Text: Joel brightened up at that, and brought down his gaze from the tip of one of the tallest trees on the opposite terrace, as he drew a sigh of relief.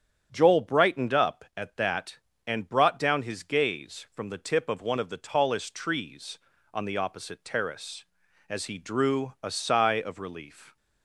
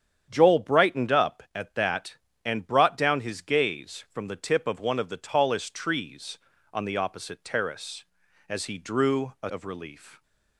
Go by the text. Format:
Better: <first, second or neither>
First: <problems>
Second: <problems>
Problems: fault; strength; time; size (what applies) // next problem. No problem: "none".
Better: first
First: starts louder than the rest; strong; until 1.3 s; 8.5 dB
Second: starts louder than the rest; strong; until 1.3 s; 9 dB // skips "sigh"; at 9.4 s